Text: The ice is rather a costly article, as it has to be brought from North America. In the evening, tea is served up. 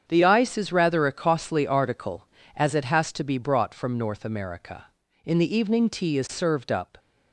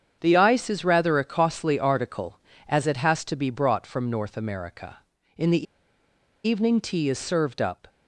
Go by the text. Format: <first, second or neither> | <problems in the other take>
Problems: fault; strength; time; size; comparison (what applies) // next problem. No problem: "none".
first | starts louder than the rest; strong; until 1.2 s; 8 dB; strong in the first // pauses between "the" and "evening"; noticeable; at 5.6 s; 0.82 s long